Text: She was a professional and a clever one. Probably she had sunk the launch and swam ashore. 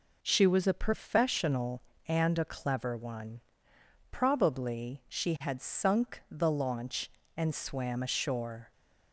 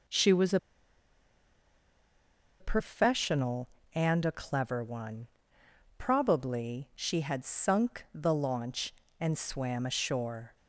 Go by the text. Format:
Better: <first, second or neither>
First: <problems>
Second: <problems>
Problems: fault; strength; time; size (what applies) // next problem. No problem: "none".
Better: first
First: none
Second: pauses between "a" and "professional"; strong; at 0.5 s; 2.0 s long